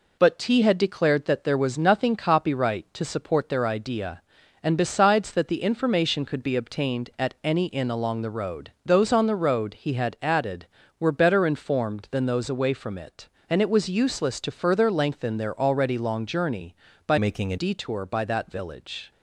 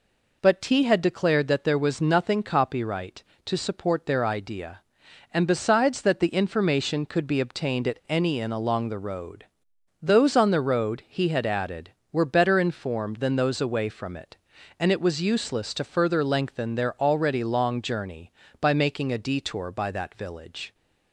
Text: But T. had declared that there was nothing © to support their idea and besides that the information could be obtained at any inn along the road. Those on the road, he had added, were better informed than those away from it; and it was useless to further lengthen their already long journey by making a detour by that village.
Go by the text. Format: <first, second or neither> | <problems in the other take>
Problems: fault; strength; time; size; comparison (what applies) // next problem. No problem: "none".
second | changes voice from "making" to "a"; from 17.1 to 17.5 s; 0.4 s long